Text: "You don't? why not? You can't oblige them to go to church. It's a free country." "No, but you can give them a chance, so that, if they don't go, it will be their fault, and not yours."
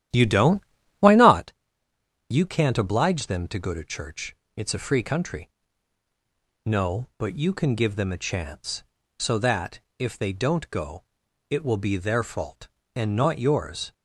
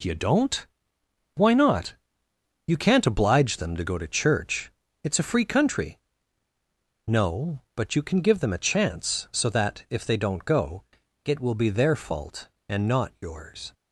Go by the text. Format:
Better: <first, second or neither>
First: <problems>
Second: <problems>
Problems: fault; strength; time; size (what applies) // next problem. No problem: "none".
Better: second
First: starts louder than the rest; strong; until 1.6 s; 12 dB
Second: none